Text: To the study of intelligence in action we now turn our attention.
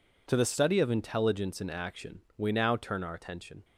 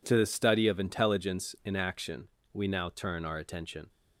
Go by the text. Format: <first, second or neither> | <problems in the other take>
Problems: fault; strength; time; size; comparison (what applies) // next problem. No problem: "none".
neither | pauses between "action" and "we"; slight; the same in both